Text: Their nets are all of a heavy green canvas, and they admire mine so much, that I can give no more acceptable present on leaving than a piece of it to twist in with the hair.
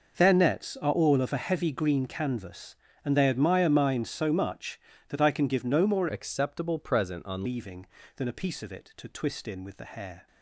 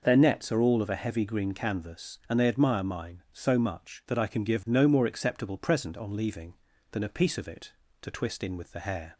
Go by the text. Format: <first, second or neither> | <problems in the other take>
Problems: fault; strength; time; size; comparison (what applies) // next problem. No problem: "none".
second | changes voice from "acceptable" to "on"; from 6.0 to 7.4 s; 1.4 s long